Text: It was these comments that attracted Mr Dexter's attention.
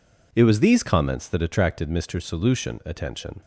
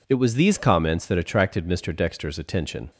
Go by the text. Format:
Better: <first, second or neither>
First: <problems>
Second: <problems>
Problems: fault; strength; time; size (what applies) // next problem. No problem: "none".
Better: second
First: says "Solution" for "Dexter's"; at 2.2 s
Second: none